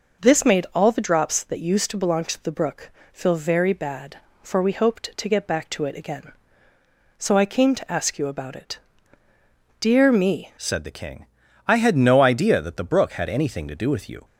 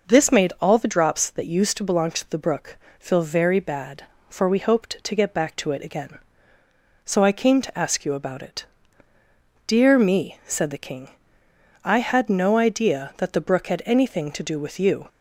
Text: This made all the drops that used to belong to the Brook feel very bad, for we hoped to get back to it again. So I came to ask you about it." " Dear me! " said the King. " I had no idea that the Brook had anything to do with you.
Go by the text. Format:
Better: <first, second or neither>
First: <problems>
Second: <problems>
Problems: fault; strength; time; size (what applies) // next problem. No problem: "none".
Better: second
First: pauses between "Brook" and "feel"; slight; at 2.9 s; 0.22 s long // changes voice at "said"; from 10.5 s on; 3.7 s long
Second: pauses between "Brook" and "feel"; slight; at 2.7 s; 0.22 s long